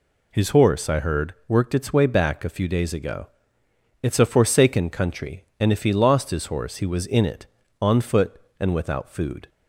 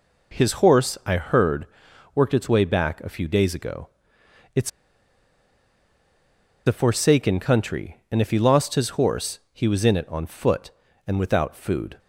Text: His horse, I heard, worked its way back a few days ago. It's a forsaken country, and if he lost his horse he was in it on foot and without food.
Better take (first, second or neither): first